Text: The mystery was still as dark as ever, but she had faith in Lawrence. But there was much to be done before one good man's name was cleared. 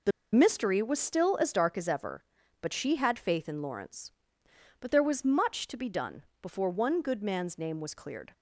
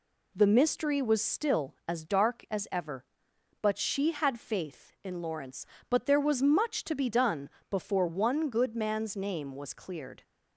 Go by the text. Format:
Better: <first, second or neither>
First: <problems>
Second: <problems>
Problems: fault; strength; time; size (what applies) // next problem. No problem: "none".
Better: second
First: pauses between "The" and "mystery"; slight; at 0.1 s; 0.23 s long // pauses between "done" and "before"; slight; at 6.2 s; 0.18 s long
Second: pauses between "done" and "before"; slight; at 7.4 s; 0.22 s long